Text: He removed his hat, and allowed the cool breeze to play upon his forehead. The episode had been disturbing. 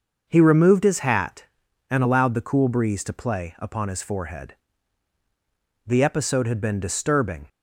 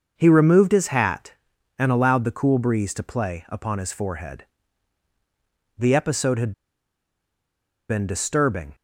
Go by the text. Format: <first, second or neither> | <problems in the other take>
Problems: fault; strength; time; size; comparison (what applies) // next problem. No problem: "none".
first | starts louder than the rest; until 1.1 s; 6 dB; also in the first // pauses between "had" and "been"; strong; at 6.5 s; 1.3 s long